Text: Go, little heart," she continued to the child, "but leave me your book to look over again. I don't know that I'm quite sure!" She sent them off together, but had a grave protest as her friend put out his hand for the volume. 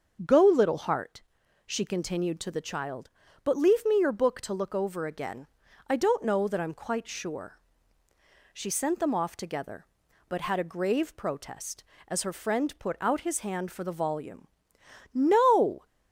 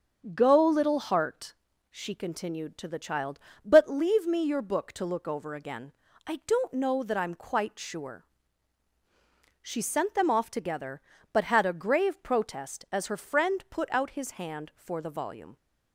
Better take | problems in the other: second | starts louder than the rest; until 1.7 s; 6.5 dB; also in the second // goes on to say "No"; noticeable; from 15.1 s on; 0.72 s long

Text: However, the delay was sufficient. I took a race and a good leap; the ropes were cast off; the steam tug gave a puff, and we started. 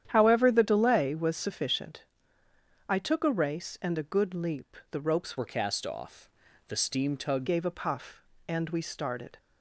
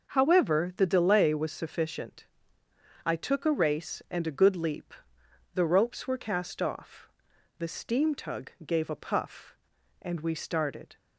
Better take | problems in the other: second | starts louder than the rest; strong; until 1.0 s; 10 dB // changes voice from "were" to "tug"; from 5.3 to 7.4 s; 2.1 s long

